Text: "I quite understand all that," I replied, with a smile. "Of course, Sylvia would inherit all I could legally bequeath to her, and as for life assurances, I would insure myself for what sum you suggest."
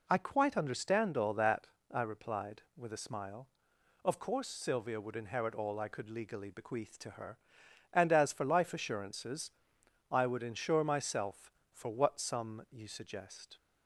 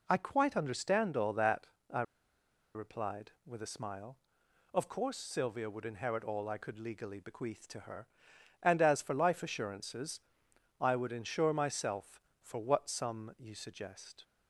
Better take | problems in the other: first | pauses between "I" and "replied"; noticeable; at 2.0 s; 0.72 s long

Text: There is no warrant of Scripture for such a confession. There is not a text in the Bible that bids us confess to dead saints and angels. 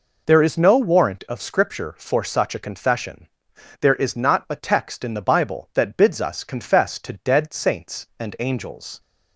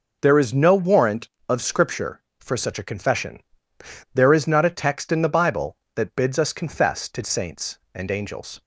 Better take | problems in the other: first | skips "dead"; at 7.2 s

